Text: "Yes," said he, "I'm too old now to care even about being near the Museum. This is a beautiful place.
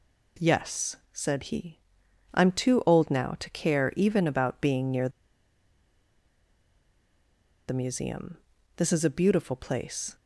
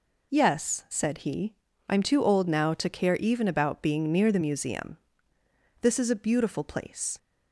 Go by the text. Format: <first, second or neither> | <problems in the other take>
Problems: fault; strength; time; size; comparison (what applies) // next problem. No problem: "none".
second | pauses between "near" and "the"; strong; at 5.0 s; 2.5 s long